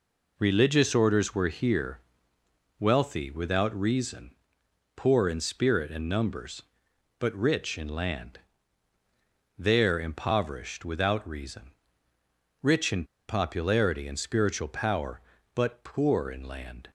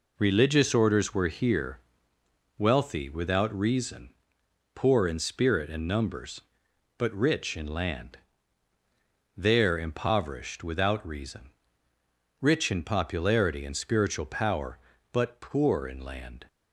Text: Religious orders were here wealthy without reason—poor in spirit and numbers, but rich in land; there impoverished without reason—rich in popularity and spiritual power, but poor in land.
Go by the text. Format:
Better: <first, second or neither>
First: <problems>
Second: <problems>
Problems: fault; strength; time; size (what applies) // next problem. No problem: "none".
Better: second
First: pauses between "here" and "wealthy"; noticeable; at 2.0 s; 0.80 s long // pauses between "in" and "popularity"; slight; at 13.0 s; 0.24 s long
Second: pauses between "here" and "wealthy"; noticeable; at 1.7 s; 0.79 s long